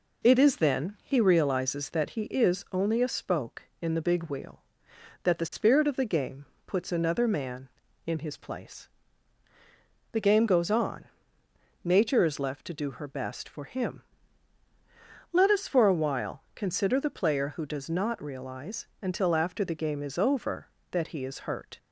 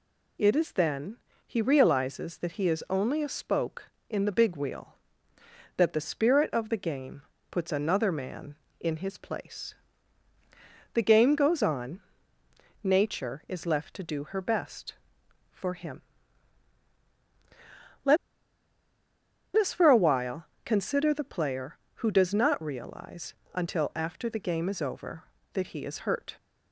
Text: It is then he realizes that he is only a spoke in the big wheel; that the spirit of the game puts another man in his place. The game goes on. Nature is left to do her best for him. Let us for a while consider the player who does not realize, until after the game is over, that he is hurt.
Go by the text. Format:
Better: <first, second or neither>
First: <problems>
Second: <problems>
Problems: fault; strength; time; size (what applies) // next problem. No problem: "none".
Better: first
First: pauses between "game" and "puts"; slight; at 6.4 s; 0.20 s long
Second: pauses between "then" and "he"; slight; at 1.1 s; 0.30 s long // pauses between "game" and "puts"; slight; at 7.2 s; 0.30 s long // pauses between "Let" and "us"; strong; at 18.1 s; 1.3 s long // pauses between "while" and "consider"; slight; at 20.4 s; 0.18 s long